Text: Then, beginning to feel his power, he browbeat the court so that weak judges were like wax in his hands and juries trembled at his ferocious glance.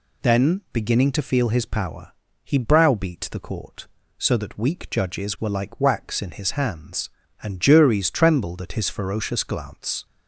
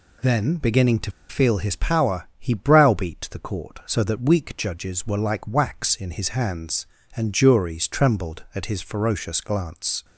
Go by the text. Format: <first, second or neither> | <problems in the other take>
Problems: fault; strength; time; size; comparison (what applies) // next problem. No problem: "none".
first | pauses between "to" and "feel"; slight; at 1.1 s; 0.18 s long